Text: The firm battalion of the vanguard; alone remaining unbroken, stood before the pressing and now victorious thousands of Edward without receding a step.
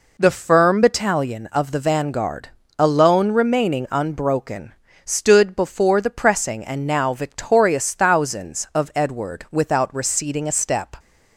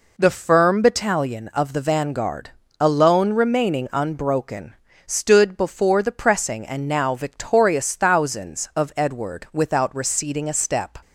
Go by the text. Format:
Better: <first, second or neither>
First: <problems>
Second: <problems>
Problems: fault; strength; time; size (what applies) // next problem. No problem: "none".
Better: neither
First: none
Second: none